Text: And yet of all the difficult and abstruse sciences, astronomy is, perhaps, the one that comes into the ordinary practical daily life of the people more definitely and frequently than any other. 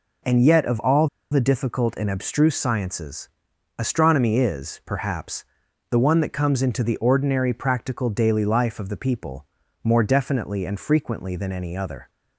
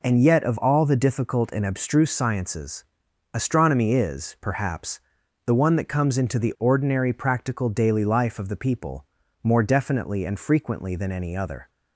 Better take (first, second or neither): second